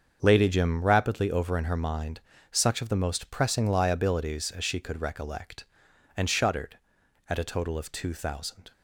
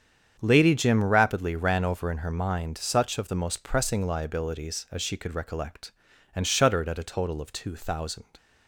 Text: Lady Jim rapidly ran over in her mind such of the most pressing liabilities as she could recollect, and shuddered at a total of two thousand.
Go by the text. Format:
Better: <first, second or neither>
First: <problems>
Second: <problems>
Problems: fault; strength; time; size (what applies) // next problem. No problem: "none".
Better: second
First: starts louder than the rest; until 1.2 s; 7 dB // skips "ran"; at 1.3 s // pauses between "mind" and "such"; slight; at 2.1 s; 0.32 s long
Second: starts louder than the rest; strong; until 1.4 s; 8 dB